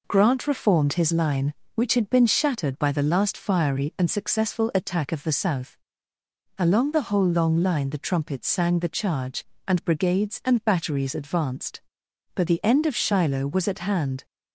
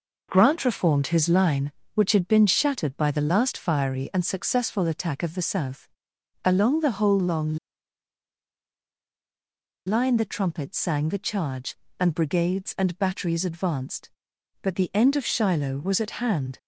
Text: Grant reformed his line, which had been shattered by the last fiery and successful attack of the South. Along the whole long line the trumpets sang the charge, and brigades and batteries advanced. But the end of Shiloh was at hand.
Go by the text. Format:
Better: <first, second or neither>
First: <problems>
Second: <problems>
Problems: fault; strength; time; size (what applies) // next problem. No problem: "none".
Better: first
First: none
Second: pauses between "long" and "line"; strong; at 7.5 s; 2.2 s long